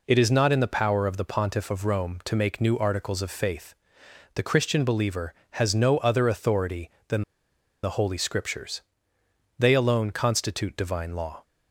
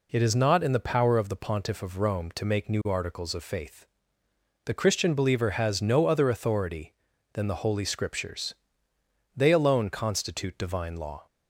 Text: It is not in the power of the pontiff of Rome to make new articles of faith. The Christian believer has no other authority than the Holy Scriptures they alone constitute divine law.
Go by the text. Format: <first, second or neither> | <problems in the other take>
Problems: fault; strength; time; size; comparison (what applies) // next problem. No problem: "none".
second | pauses between "than" and "the"; noticeable; at 7.2 s; 0.61 s long // pauses between "Scriptures" and "they"; noticeable; at 8.8 s; 0.78 s long; noticeable in the second